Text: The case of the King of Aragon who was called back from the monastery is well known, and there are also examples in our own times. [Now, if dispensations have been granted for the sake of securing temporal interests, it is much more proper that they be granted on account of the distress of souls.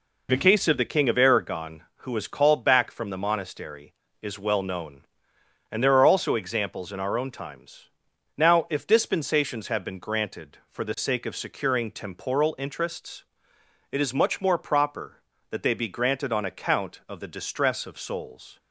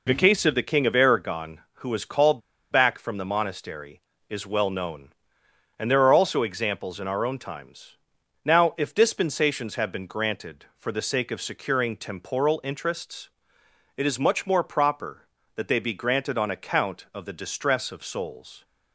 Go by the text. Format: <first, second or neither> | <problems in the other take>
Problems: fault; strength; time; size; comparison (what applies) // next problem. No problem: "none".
first | pauses between "called" and "back"; slight; at 2.4 s; 0.30 s long